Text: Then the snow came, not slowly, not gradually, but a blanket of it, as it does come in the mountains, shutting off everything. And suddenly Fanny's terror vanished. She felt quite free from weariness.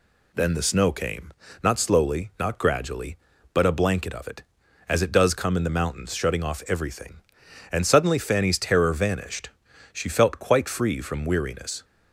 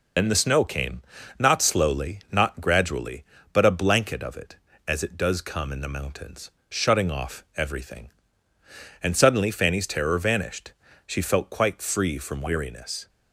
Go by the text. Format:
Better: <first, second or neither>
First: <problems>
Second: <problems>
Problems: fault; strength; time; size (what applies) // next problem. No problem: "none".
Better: first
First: none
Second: loses the start of "Then"; at 0.1 s; 55 ms